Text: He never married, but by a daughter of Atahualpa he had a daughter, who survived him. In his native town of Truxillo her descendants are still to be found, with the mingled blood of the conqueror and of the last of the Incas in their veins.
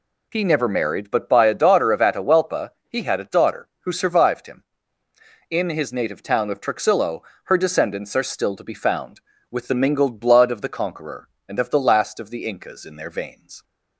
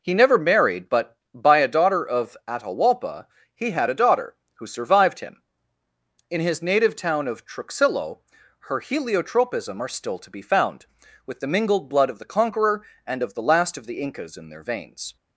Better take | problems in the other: first | pauses between "Atahualpa" and "he"; slight; at 3.2 s; 0.26 s long; slight in the first // pauses between "Truxillo" and "her"; noticeable; at 8.1 s; 0.50 s long; slight in the first // says "heliotropism" for "descendants"; at 8.7 s

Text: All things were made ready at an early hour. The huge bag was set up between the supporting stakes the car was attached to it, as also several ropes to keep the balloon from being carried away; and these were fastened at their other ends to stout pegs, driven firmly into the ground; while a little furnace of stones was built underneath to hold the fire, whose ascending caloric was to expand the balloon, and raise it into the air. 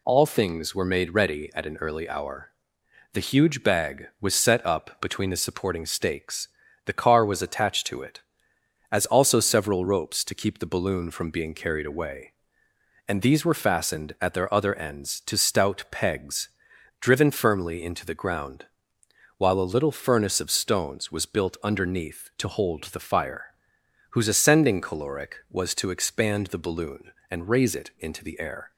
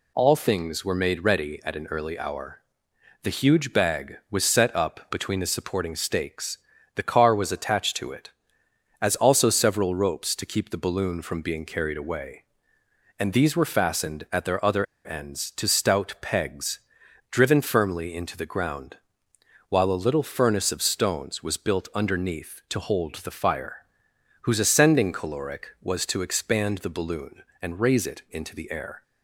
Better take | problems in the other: first | pauses between "stakes" and "the"; slight; at 6.5 s; 0.36 s long; slight in the first // pauses between "other" and "ends"; slight; at 14.8 s; 0.19 s long

